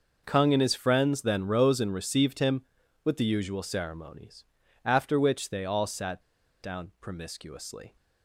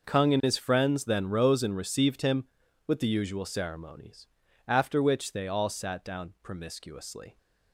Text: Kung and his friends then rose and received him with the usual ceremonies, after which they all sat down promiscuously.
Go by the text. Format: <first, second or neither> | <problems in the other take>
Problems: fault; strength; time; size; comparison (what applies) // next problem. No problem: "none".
second | pauses between "sat" and "down"; at 6.2 s; 0.41 s long